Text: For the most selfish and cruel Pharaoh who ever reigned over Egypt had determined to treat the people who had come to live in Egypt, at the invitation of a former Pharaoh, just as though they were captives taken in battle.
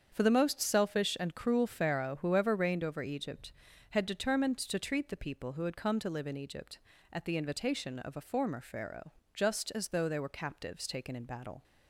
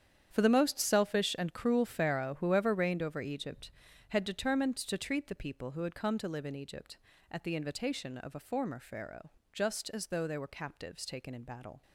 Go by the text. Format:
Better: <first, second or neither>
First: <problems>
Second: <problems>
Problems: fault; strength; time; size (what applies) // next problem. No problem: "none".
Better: first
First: starts louder than the rest; strong; until 1.1 s; 7.5 dB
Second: gets quieter; strong; throughout; 13.5 dB // starts louder than the rest; strong; until 1.3 s; 9 dB